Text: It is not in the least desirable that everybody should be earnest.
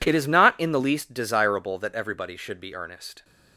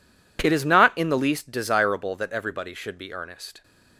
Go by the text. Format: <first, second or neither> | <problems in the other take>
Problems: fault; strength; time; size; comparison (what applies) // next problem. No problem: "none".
neither | none